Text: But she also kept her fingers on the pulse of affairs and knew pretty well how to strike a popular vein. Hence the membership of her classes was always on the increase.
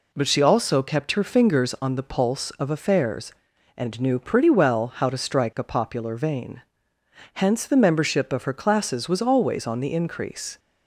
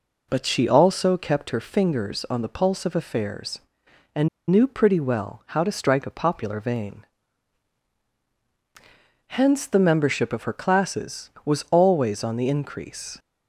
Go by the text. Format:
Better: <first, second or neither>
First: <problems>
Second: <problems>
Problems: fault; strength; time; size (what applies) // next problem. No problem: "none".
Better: first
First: none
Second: pauses between "and" and "knew"; slight; at 4.2 s; 0.22 s long